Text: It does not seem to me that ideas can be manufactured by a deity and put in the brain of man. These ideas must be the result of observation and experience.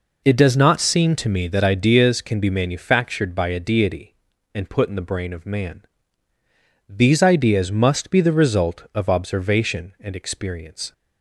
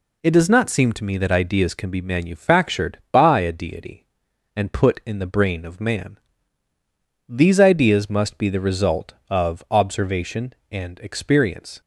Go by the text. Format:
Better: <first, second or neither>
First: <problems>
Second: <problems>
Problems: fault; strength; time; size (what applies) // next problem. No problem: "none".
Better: neither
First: none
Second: none